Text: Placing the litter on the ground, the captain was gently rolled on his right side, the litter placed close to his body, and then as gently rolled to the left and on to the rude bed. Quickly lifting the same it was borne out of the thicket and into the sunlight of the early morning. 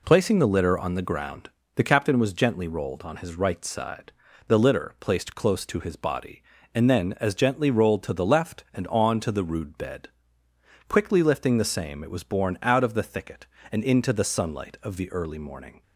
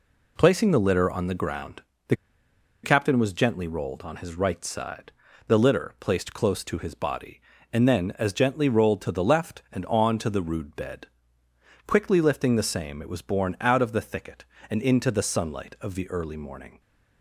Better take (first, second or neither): first